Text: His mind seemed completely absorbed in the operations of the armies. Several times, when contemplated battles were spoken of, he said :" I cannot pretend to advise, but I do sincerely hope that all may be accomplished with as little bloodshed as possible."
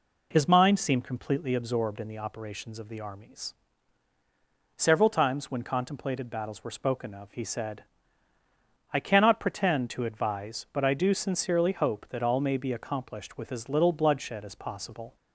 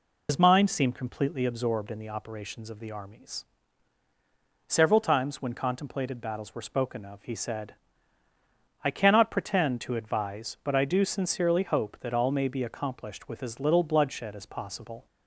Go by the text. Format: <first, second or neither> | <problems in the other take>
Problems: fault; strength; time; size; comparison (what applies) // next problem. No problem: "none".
first | loses the start of "His"; at 0.2 s; 80 ms